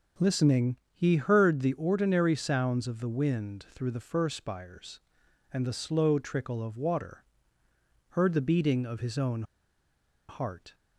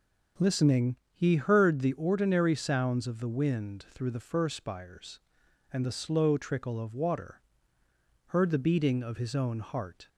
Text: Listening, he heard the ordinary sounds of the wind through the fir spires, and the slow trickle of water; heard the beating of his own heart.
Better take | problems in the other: second | pauses between "own" and "heart"; noticeable; at 9.4 s; 0.85 s long

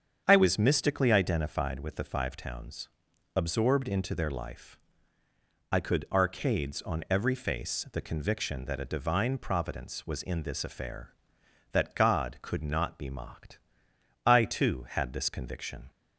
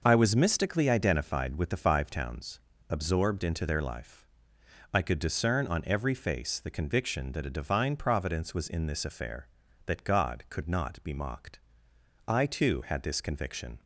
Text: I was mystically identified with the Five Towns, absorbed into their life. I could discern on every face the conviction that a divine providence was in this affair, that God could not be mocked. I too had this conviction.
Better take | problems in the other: second | starts louder than the rest; strong; until 1.2 s; 7.5 dB // says "arcades" for "discern"; at 6.1 s

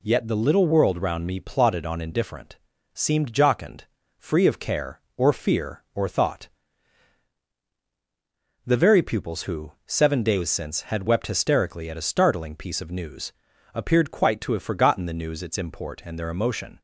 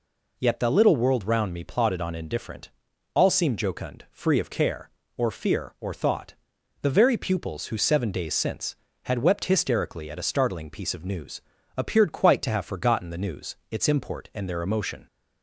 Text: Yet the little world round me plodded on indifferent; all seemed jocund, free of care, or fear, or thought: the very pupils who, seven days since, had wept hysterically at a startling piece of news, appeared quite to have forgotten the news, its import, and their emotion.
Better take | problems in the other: second | skips "all"; at 2.7 s

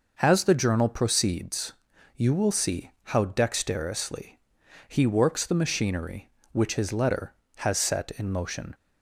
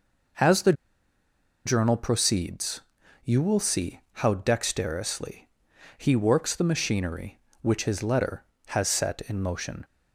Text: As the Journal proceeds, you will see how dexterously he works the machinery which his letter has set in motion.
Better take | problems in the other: first | pauses between "the" and "Journal"; noticeable; at 0.7 s; 0.92 s long // pauses between "dexterously" and "he"; noticeable; at 5.4 s; 0.48 s long; noticeable in the first

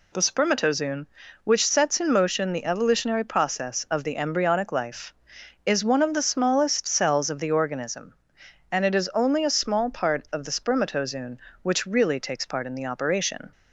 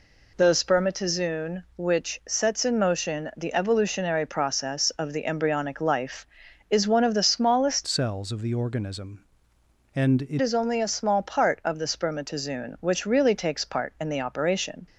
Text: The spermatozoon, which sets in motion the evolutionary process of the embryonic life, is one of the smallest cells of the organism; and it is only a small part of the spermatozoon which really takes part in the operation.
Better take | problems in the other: first | changes voice from "cells" to "it"; from 7.8 to 10.3 s; 2.5 s long

